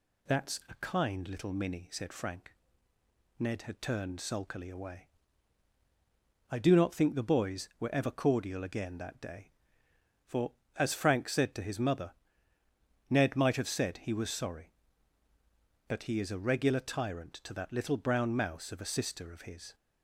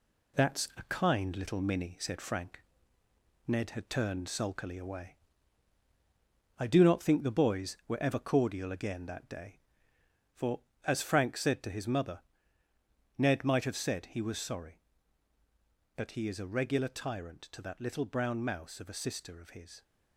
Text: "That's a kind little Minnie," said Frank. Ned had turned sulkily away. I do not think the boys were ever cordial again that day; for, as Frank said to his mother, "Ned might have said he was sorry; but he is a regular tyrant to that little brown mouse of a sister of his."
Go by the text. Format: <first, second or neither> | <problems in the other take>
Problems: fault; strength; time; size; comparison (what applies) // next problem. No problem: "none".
first | gets quieter; noticeable; throughout; 4.5 dB